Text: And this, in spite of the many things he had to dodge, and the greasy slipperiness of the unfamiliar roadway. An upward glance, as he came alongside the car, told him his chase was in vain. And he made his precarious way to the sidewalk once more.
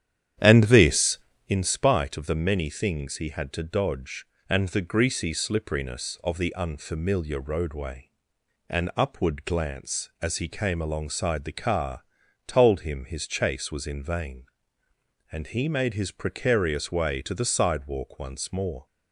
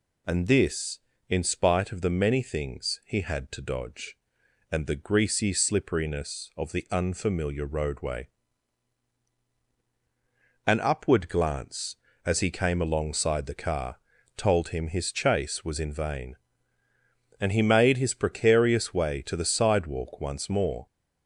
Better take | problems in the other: second | starts louder than the rest; strong; until 1.6 s; 9.5 dB

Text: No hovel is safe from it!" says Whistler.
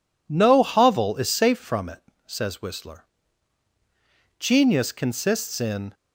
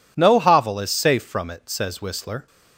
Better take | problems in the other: second | goes on to say "Genius consists in"; from 4.3 s on; 1.5 s long

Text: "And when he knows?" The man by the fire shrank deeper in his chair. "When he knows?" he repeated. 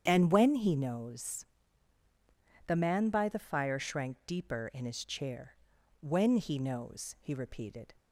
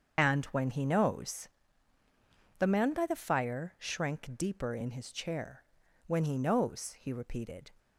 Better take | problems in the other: first | loses the start of "And"; at 0.1 s; 40 ms // starts louder than the rest; strong; until 1.2 s; 7 dB; strong in the first

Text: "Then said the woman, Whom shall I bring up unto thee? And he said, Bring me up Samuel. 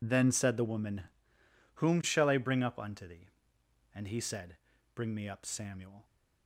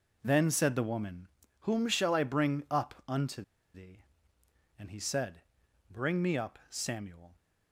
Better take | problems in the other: first | pauses between "unto" and "thee"; slight; at 3.4 s; 0.32 s long

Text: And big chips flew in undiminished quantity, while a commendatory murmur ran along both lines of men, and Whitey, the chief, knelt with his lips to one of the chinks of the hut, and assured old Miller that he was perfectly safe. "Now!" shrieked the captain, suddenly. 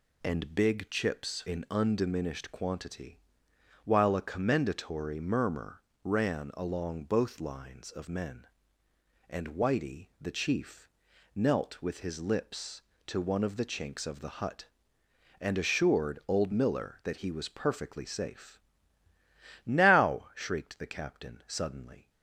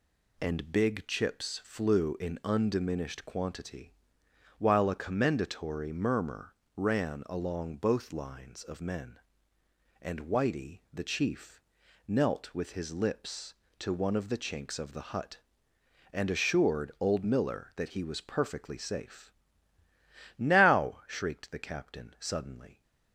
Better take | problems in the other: second | skips "flew"; at 1.4 s // pauses between "murmur" and "ran"; slight; at 5.7 s; 0.24 s long; slight in the second

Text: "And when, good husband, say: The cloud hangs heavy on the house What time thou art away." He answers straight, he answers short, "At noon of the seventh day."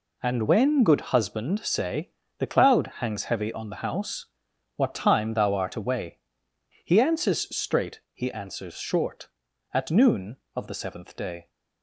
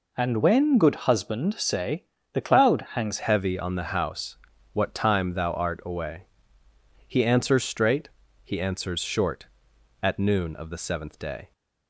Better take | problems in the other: first | changes voice at "heavy"; from 3.1 s on; 8.4 s long // pauses between "house" and "What"; at 4.3 s; 0.38 s long; noticeable in the first

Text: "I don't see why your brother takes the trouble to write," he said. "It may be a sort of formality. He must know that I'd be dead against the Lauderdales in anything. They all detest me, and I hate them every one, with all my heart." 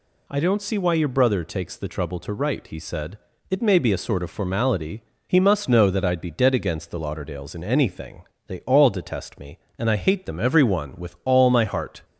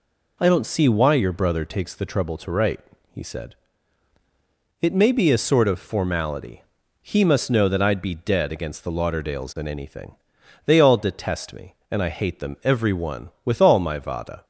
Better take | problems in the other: first | says "vada" for "heart"; at 13.9 s

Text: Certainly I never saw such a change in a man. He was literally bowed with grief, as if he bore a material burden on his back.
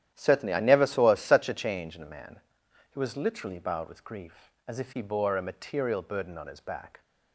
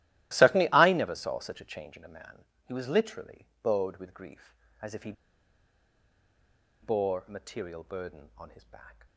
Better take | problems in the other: first | starts louder than the rest; strong; until 1.3 s; 15.5 dB; strong in the first // pauses between "literally" and "bowed"; slight; at 3.4 s; 0.18 s long // pauses between "he" and "bore"; strong; at 5.1 s; 1.7 s long

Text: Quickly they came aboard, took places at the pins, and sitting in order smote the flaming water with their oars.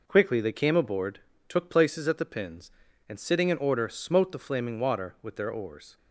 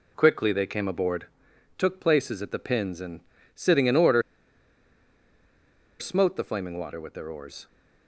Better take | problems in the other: first | pauses between "and" and "sitting"; slight; at 3.1 s; 0.34 s long // pauses between "order" and "smote"; strong; at 4.2 s; 1.7 s long

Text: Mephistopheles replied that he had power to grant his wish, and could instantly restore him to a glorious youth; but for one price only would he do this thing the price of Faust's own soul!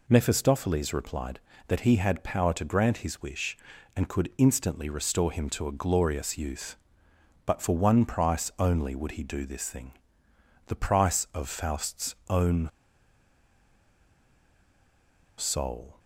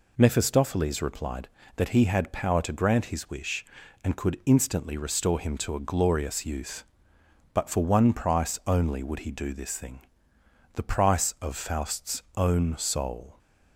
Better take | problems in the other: second | pauses between "thing" and "the"; noticeable; at 9.9 s; 0.74 s long; noticeable in the second // pauses between "own" and "soul"; strong; at 12.6 s; 2.6 s long

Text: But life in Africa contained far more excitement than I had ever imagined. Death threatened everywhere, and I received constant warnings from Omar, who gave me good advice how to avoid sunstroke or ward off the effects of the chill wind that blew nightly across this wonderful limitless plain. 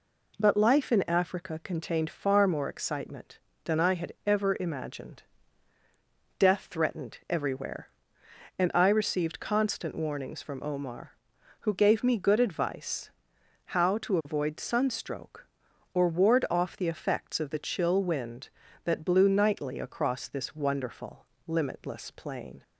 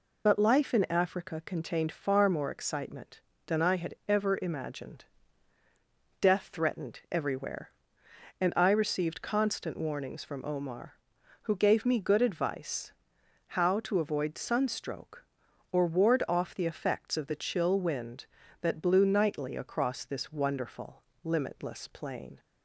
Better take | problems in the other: first | loses the start of "But"; at 0.2 s; 90 ms // pauses between "advice" and "how"; noticeable; at 12.9 s; 0.58 s long; noticeable in the first // pauses between "wonderful" and "limitless"; slight; at 21.0 s; 0.20 s long; slight in the first

